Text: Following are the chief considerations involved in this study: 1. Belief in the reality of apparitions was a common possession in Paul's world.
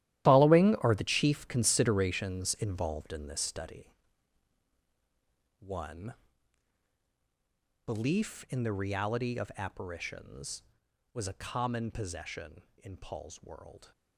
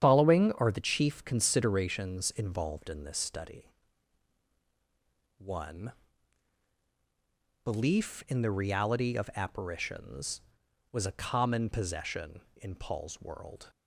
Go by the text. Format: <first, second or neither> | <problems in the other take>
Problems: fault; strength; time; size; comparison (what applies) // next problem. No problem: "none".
second | gets quieter; strong; throughout; 13.5 dB // starts louder than the rest; strong; until 1.3 s; 13.5 dB; strong in the second